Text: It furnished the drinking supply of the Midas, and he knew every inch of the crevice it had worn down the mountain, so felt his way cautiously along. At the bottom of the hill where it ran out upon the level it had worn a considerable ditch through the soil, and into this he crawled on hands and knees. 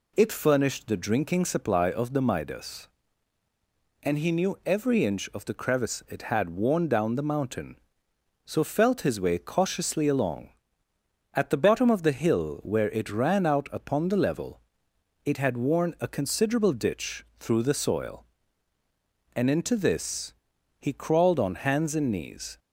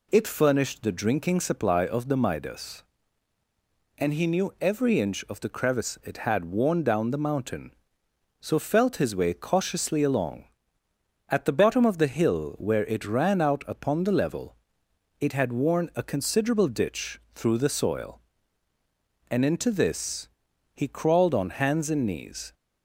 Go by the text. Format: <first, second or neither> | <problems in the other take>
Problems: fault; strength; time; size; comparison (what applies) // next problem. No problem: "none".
neither | pauses between "level" and "it"; noticeable; the same in both // pauses between "ditch" and "through"; slight; the same in both // pauses between "this" and "he"; noticeable; the same in both